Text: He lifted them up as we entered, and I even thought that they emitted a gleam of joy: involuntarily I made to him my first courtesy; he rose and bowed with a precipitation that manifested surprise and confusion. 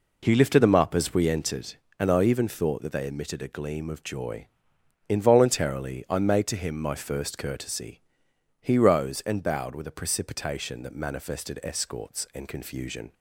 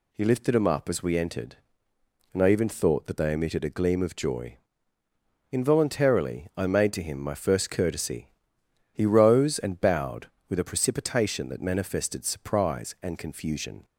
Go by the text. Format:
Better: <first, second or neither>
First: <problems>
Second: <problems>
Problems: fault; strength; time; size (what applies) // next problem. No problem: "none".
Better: second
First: says "escorts" for "surprise"; at 11.6 s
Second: none